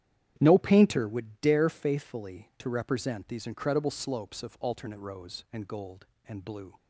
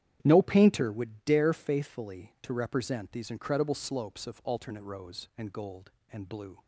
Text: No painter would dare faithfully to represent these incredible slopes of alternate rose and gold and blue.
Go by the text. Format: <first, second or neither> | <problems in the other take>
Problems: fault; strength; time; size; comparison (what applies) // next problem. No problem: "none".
neither | starts louder than the rest; strong; the same in both